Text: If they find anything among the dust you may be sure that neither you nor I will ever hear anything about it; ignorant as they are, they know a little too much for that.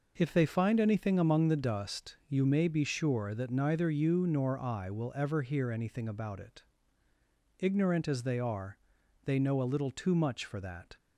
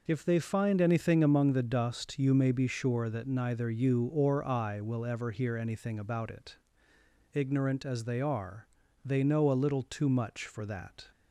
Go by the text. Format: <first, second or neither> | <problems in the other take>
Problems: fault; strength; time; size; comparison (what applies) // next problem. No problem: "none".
first | says "or" for "nor"; at 4.0 s